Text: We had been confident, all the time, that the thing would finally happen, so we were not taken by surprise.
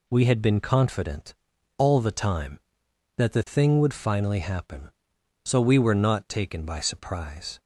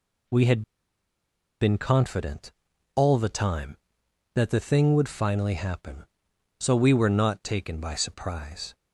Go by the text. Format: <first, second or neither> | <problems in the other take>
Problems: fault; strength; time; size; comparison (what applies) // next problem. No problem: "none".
first | pauses between "had" and "been"; at 0.6 s; 0.99 s long